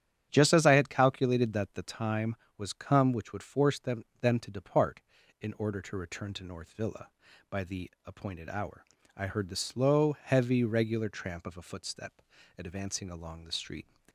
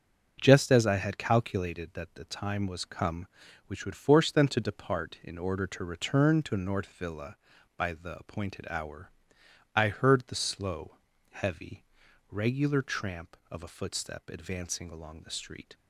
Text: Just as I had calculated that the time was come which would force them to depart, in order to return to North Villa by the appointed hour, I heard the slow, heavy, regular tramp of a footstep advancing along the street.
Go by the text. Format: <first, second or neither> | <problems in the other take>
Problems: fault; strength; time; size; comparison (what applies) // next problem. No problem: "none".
second | starts louder than the rest; strong; until 1.3 s; 9.5 dB; also in the second // says "them" twice; at 4.2 s // pauses between "footstep" and "advancing"; slight; at 12.2 s; 0.34 s long